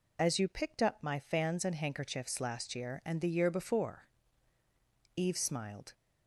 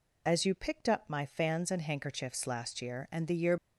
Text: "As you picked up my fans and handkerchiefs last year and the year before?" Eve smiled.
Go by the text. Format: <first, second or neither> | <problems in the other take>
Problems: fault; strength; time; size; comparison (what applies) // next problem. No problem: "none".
first | stops before "before Eve smiled"; at 3.5 s